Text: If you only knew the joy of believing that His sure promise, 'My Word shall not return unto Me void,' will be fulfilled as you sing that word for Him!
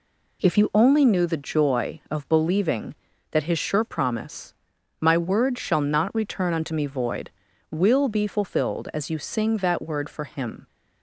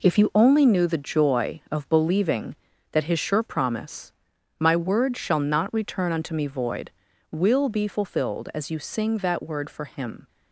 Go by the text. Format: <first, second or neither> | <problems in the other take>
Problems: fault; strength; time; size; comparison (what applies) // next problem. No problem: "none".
first | gets quieter; strong; throughout; 7 dB